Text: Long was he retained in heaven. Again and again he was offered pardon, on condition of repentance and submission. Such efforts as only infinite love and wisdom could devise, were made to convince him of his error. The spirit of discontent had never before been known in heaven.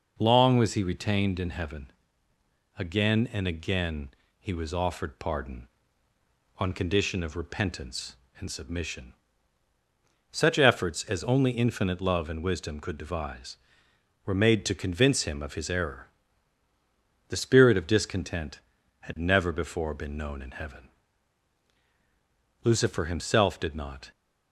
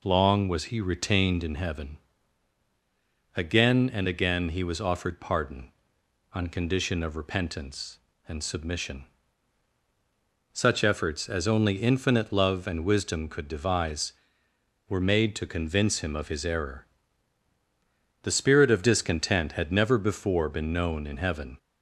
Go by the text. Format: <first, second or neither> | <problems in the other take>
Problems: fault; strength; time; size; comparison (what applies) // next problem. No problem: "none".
second | pauses between "again" and "he"; slight; at 4.1 s; 0.28 s long // goes on to say "Lucifer himself did not"; from 22.6 s on; 1.4 s long